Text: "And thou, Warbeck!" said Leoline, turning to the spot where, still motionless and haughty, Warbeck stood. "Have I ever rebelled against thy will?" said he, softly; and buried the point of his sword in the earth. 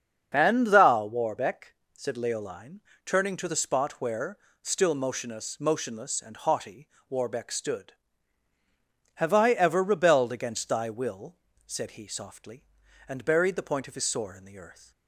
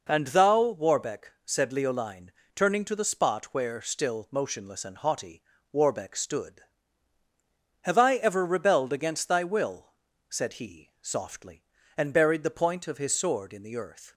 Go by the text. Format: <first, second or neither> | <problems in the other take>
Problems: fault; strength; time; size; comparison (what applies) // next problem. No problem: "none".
second | starts louder than the rest; until 1.3 s; 7 dB // says "motionless" twice; at 5.5 s